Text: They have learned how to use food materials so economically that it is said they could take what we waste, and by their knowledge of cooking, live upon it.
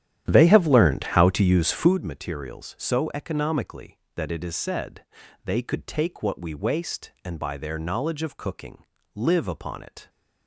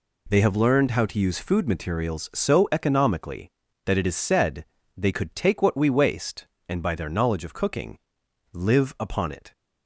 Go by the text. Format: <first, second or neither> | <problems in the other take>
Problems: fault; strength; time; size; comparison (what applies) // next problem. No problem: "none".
second | starts louder than the rest; strong; until 2.0 s; 11 dB // pauses between "said" and "they"; at 5.0 s; 0.40 s long; slight in the second